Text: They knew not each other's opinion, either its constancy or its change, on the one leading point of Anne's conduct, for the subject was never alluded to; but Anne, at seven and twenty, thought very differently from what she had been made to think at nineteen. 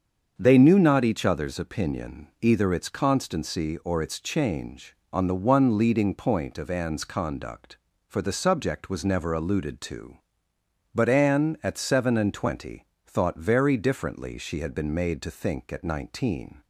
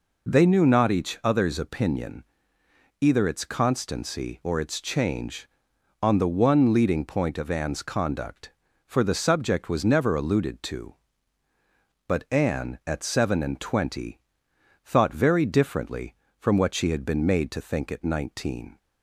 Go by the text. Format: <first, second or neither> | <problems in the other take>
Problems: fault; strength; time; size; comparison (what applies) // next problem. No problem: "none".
second | starts louder than the rest; until 1.3 s; 7 dB // skips "from what"; at 14.3 s